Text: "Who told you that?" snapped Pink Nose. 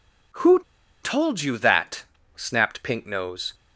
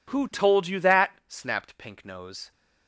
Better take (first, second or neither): second